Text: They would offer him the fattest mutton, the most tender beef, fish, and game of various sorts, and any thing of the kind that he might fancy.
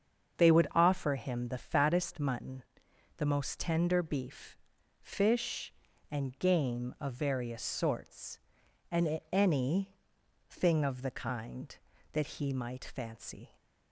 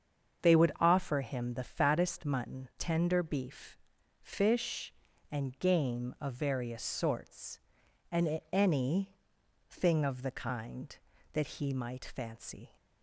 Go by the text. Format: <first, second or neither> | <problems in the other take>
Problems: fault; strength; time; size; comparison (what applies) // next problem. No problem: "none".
first | starts louder than the rest; until 1.4 s; 7 dB; strong in the first // skips "the most"; at 2.7 s // pauses between "any" and "thing"; noticeable; at 9.1 s; 0.54 s long; noticeable in the first